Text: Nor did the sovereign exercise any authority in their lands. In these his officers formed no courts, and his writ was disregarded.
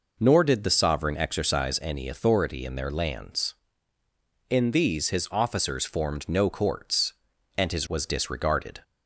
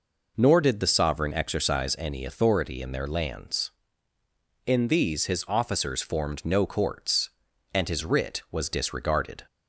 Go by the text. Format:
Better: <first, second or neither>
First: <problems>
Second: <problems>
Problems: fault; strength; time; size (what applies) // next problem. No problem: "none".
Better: second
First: skips "writ"; at 7.8 s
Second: none